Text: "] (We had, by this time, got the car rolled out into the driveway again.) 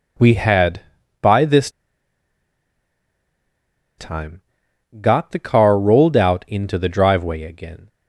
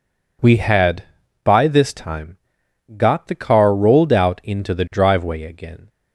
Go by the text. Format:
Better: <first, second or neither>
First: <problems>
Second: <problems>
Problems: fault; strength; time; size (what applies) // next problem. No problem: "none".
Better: second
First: pauses between "this" and "time"; strong; at 1.6 s; 2.2 s long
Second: none